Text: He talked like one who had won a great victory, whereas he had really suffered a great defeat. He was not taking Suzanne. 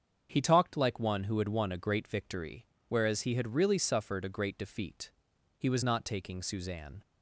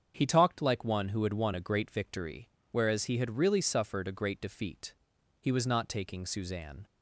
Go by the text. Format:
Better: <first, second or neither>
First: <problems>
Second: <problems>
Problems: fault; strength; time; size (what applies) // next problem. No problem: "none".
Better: neither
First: starts louder than the rest; strong; until 1.3 s; 7 dB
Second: starts louder than the rest; strong; until 1.1 s; 7 dB